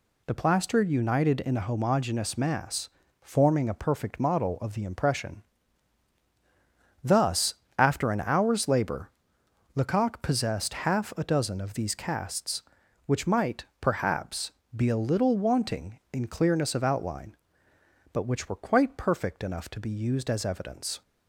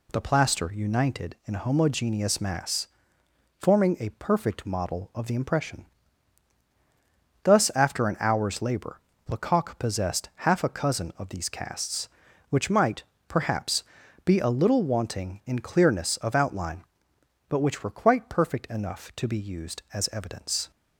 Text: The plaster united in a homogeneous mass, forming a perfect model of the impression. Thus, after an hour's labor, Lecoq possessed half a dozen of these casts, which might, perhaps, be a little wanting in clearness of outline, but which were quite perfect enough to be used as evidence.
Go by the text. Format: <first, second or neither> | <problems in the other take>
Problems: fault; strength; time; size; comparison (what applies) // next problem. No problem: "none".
first | says "cousin" for "dozen"; at 10.6 s